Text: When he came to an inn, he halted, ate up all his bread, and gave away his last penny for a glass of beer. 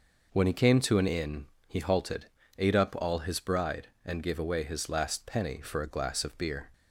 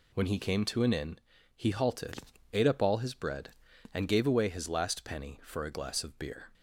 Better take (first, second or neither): second